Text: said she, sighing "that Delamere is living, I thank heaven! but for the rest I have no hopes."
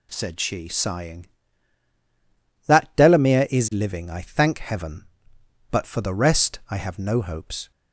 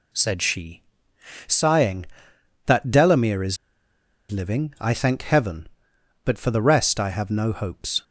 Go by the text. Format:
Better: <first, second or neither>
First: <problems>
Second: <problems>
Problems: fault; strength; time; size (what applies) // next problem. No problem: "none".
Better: first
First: none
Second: pauses between "is" and "living"; noticeable; at 3.5 s; 0.74 s long